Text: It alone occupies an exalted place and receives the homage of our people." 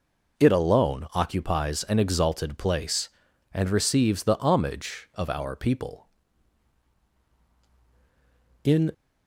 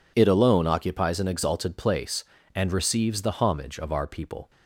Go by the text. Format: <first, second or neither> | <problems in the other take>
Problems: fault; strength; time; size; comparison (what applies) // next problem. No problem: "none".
second | goes on to say "In"; slight; from 8.6 s on; 0.28 s long